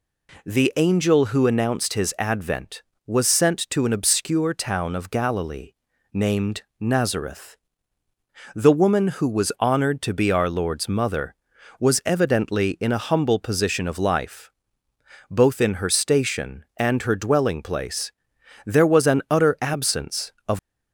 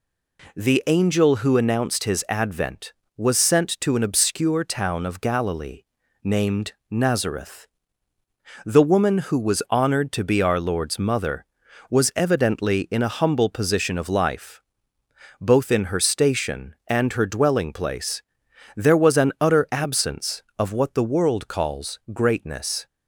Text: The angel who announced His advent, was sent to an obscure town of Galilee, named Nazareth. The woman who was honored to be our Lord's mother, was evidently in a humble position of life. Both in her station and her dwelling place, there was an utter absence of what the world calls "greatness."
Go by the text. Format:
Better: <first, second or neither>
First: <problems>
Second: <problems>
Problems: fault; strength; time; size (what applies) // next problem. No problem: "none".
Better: second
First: pauses between "named" and "Nazareth"; slight; at 6.6 s; 0.16 s long // stops before "what the world calls greatness"; at 20.5 s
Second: pauses between "named" and "Nazareth"; slight; at 6.7 s; 0.16 s long